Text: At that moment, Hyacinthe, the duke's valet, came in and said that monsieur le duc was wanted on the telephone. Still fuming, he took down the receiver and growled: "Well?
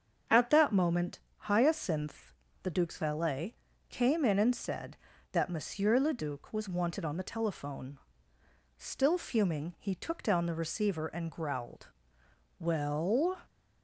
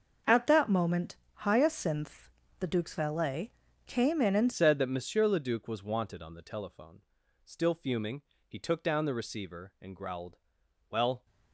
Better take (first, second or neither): first